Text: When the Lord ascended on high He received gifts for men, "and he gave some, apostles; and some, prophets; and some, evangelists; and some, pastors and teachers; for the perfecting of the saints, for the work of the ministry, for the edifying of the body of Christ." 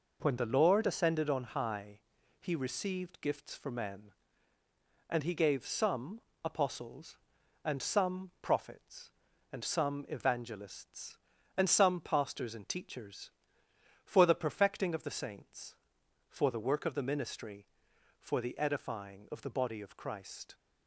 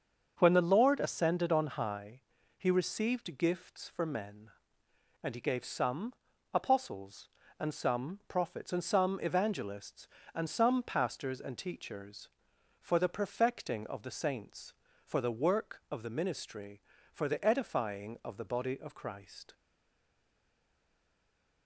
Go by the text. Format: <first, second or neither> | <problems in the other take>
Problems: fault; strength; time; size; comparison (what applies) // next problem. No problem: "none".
first | starts louder than the rest; until 1.3 s; 7 dB // pauses between "high" and "He"; at 2.1 s; 0.38 s long; noticeable in the first // stays silent after the last word; from 19.5 s on; 2.1 s long